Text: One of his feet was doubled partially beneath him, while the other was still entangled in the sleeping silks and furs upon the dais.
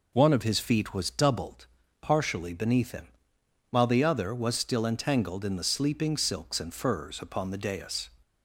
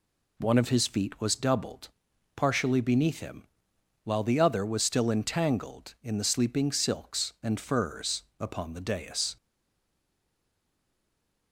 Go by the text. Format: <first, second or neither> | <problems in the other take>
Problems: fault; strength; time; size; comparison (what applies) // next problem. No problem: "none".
first | pauses between "doubled" and "partially"; noticeable; at 1.8 s; 0.46 s long; slight in the first // pauses between "furs" and "upon"; slight; at 8.2 s; 0.18 s long // stays silent after the last word; from 9.3 s on; 2.2 s long